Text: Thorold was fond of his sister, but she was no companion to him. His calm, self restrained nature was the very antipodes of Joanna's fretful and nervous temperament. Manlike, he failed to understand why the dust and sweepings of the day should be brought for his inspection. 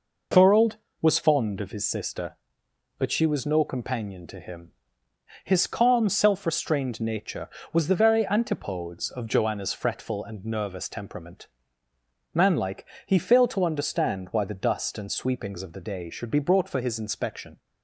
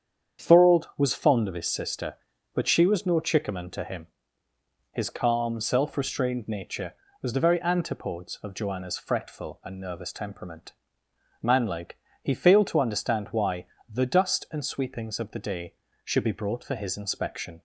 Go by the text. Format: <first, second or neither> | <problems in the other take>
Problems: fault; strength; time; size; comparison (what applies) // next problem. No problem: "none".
first | starts louder than the rest; strong; until 1.4 s; 8 dB // says "chickaman" for "companion"; at 3.1 s // pauses between "why" and "the"; slight; at 13.6 s; 0.24 s long